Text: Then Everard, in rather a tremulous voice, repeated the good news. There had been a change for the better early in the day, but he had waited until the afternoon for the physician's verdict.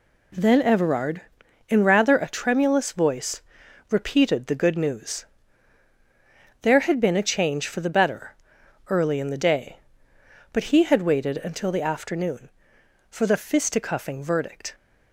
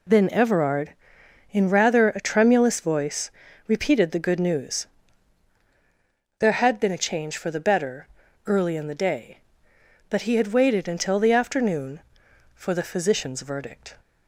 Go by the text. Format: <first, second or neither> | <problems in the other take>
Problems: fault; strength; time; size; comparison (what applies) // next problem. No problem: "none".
second | pauses between "better" and "early"; noticeable; at 8.3 s; 0.56 s long; also in the second // says "fisticuffing" for "physician's"; at 13.3 s